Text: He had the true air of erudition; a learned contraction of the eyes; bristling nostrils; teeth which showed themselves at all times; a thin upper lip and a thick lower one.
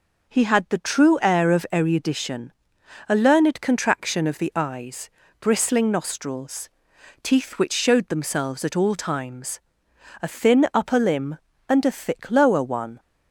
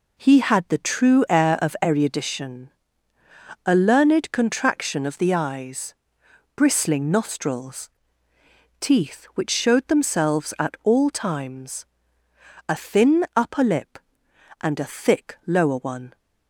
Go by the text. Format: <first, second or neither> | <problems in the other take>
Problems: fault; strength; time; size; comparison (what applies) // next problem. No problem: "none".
second | says "limb" for "lip"; at 10.9 s